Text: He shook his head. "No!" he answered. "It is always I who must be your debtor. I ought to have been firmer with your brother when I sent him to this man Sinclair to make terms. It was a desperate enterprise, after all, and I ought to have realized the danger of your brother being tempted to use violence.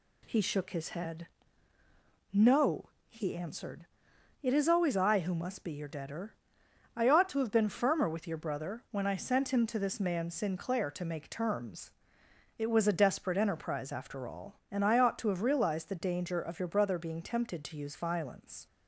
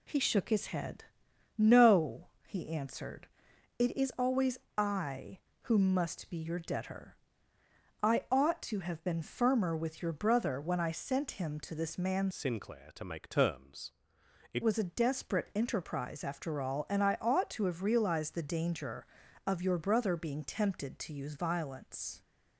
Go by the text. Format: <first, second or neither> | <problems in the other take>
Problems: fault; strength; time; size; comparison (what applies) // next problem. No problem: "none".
first | pauses between "always" and "I"; slight; at 4.5 s; 0.20 s long // changes voice from "Sinclair" to "It"; from 12.3 to 14.6 s; 2.3 s long